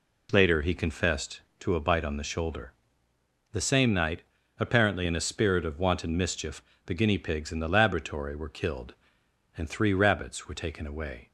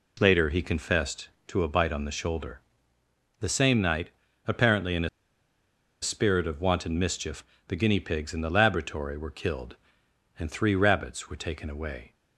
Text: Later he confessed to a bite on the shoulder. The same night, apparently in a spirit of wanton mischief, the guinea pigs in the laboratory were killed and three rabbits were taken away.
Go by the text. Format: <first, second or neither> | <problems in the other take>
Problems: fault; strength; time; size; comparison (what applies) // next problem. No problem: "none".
first | pauses between "a" and "spirit"; noticeable; at 5.0 s; 0.94 s long